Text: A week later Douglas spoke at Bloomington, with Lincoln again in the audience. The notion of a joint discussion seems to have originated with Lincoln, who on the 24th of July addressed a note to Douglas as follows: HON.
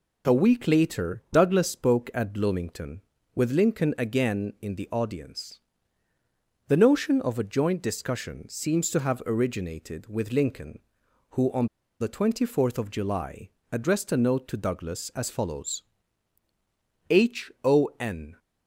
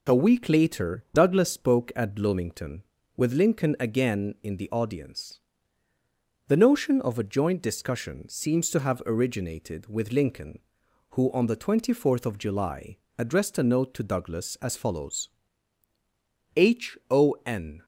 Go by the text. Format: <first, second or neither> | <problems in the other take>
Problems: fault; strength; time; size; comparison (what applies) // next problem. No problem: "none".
second | pauses between "on" and "the"; slight; at 11.6 s; 0.32 s long // pauses between "July" and "addressed"; slight; at 13.5 s; 0.20 s long; slight in the second